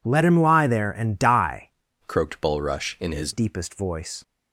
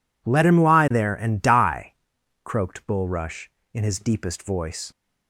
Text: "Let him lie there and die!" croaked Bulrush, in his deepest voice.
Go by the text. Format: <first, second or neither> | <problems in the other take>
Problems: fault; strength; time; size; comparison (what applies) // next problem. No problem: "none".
second | changes voice from "croaked" to "his"; from 2.0 to 3.3 s; 1.3 s long